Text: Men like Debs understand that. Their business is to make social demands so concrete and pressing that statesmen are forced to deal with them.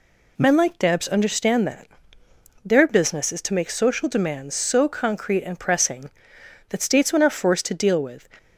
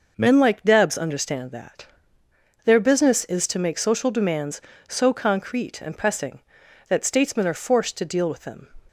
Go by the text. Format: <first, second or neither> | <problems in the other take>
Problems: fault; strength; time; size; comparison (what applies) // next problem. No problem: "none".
second | stops before "them"; at 8.3 s